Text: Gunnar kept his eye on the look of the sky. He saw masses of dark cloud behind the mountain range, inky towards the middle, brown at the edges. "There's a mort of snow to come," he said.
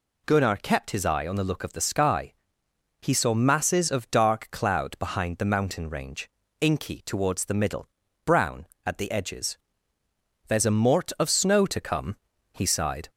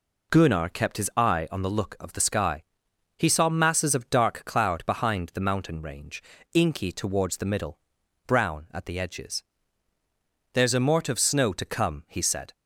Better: second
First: says "sighed" for "said"; at 12.6 s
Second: none

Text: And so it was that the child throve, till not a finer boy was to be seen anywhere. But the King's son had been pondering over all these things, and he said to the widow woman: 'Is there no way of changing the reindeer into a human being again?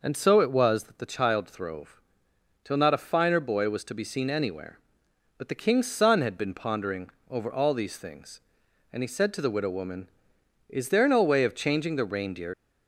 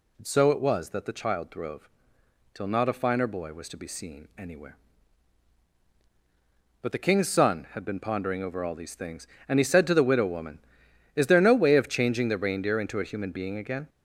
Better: second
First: pauses between "pondering" and "over"; slight; at 7.0 s; 0.20 s long // stops before "into a human being again"; at 12.5 s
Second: none

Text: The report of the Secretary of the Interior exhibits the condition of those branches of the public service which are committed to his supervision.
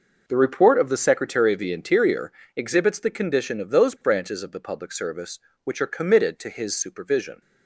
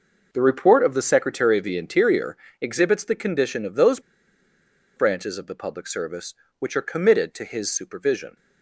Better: first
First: pauses between "Interior" and "exhibits"; slight; at 2.3 s; 0.24 s long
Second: pauses between "Interior" and "exhibits"; slight; at 2.3 s; 0.24 s long // pauses between "those" and "branches"; noticeable; at 3.9 s; 0.97 s long

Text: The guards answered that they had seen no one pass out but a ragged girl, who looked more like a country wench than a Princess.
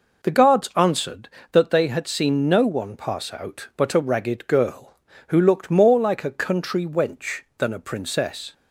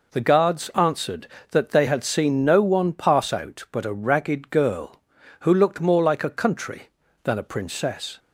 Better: first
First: none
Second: skips "wench"; at 7.0 s

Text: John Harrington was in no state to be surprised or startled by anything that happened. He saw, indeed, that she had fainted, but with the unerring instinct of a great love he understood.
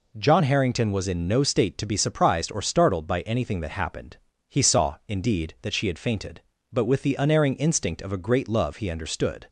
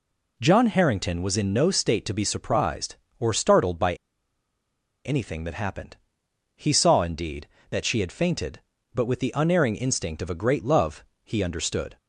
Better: first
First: none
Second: pauses between "by" and "anything"; at 3.9 s; 1.1 s long // pauses between "love" and "he"; slight; at 11.0 s; 0.18 s long

